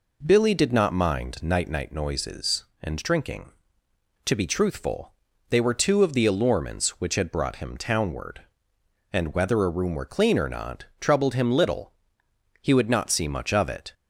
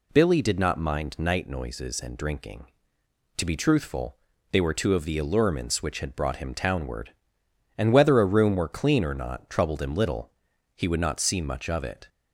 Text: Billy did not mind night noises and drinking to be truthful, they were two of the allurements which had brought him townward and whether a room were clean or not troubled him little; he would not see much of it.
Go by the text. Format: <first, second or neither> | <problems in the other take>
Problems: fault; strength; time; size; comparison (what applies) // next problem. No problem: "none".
second | says "night" twice; at 1.6 s